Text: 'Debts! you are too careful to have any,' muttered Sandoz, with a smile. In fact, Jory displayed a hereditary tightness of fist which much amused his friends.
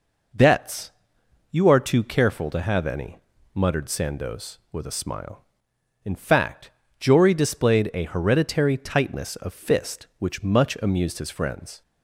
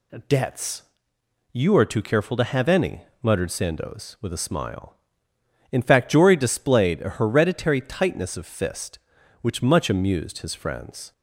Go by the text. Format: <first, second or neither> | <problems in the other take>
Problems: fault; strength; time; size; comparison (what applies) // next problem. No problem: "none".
neither | none